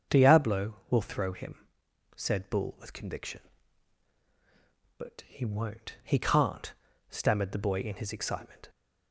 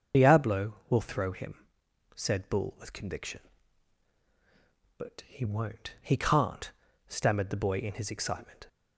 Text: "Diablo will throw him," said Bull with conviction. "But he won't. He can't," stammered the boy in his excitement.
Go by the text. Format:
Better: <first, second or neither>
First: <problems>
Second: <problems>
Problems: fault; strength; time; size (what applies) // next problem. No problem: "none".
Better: first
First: starts louder than the rest; until 1.2 s; 7 dB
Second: loses the start of "Diablo"; at 0.1 s; 55 ms // starts louder than the rest; until 1.2 s; 6.5 dB